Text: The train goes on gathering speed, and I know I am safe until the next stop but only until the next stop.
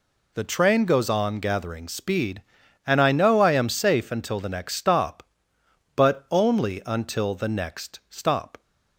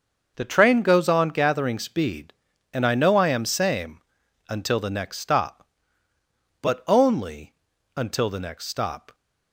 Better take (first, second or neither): first